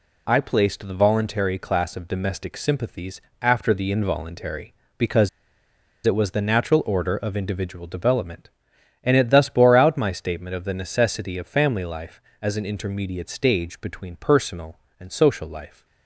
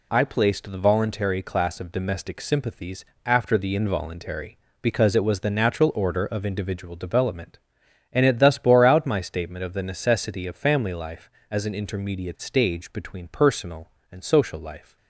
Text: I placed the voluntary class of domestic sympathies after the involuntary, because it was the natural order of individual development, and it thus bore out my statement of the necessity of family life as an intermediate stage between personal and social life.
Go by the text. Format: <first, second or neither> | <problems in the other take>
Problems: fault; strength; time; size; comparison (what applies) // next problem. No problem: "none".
second | pauses between "sympathies" and "after"; slight; at 3.2 s; 0.20 s long; slight in the second // pauses between "because" and "it"; noticeable; at 5.2 s; 0.75 s long